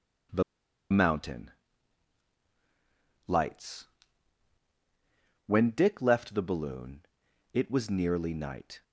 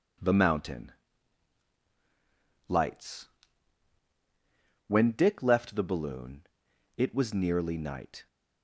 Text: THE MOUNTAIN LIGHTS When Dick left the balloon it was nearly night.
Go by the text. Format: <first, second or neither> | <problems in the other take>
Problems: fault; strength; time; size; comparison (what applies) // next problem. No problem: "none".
second | pauses between "THE" and "MOUNTAIN"; noticeable; at 0.4 s; 0.49 s long // pauses between "MOUNTAIN" and "LIGHTS"; strong; at 1.4 s; 1.7 s long; strong in the second // pauses between "LIGHTS" and "When"; strong; at 3.8 s; 1.6 s long; strong in the second // pauses between "balloon" and "it"; noticeable; at 7.0 s; 0.52 s long; noticeable in the second